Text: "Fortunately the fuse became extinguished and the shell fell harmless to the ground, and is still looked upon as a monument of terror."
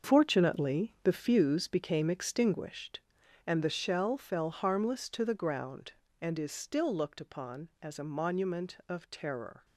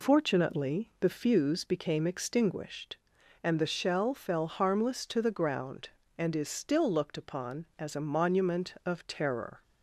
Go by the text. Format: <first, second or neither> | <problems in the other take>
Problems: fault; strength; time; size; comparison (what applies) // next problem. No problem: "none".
second | gets quieter; strong; throughout; 10.5 dB